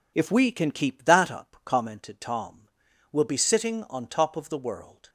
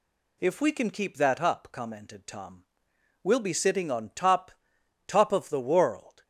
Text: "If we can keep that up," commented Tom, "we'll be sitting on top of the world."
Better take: first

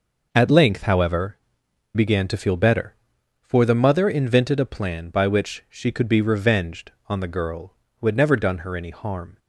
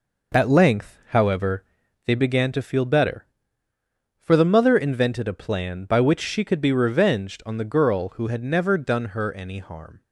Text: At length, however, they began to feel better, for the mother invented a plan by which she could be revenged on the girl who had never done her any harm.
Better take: second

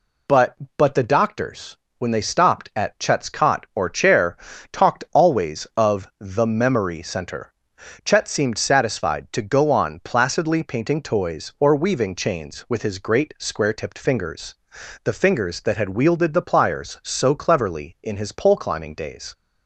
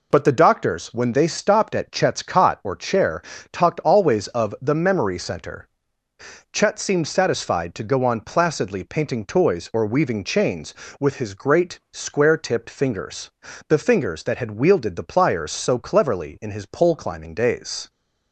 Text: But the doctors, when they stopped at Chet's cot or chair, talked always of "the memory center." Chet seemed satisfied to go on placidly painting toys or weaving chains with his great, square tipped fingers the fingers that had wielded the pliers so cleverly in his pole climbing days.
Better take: second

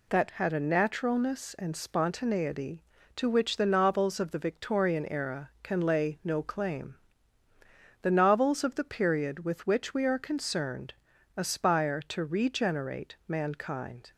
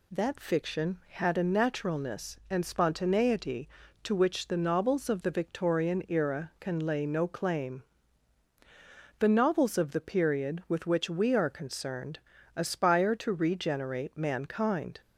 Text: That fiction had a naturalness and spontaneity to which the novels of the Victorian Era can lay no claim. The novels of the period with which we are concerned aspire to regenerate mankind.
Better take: second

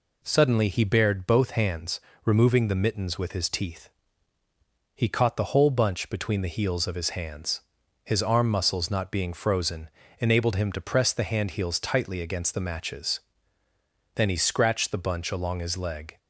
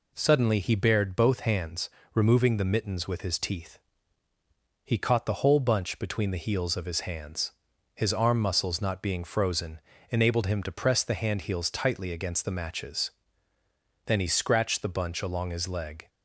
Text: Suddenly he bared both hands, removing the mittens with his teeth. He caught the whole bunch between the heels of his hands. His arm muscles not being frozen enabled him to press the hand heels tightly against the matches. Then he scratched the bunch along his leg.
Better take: neither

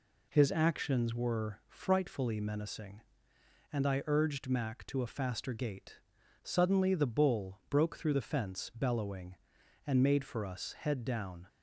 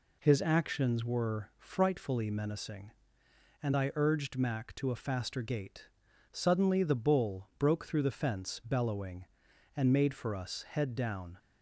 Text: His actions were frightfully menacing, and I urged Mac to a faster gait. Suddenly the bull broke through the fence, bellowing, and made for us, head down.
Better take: neither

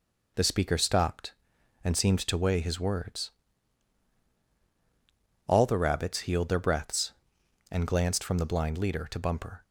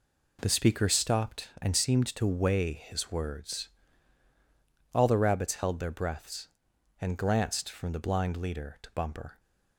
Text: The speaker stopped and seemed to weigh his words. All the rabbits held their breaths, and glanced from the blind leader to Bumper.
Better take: second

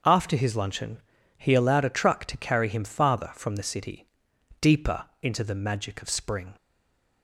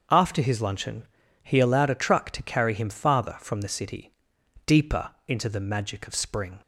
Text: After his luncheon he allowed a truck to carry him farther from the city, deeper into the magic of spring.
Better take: second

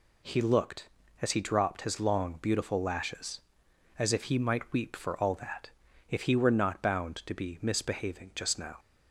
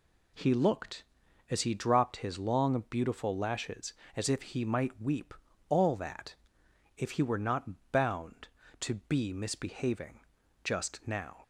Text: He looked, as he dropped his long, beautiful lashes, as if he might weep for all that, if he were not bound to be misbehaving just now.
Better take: first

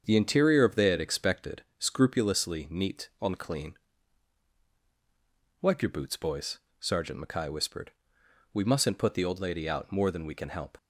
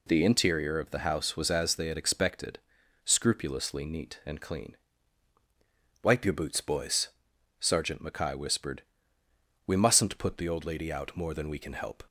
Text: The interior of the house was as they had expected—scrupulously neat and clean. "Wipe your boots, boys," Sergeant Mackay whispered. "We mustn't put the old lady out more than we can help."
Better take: second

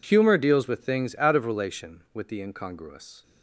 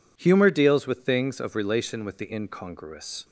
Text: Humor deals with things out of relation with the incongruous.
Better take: first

